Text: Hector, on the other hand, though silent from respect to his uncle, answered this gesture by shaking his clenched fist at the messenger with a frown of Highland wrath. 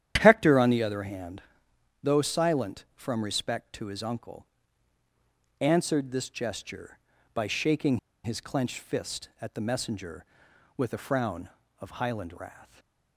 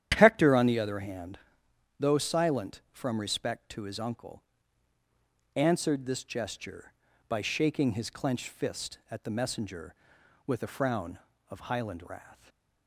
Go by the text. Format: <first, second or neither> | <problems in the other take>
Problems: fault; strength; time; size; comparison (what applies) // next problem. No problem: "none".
second | starts louder than the rest; strong; until 1.2 s; 10.5 dB; strong in the second // pauses between "shaking" and "his"; slight; at 7.9 s; 0.25 s long // stays silent after the last word; slight; from 12.6 s on; 0.5 s long; slight in the second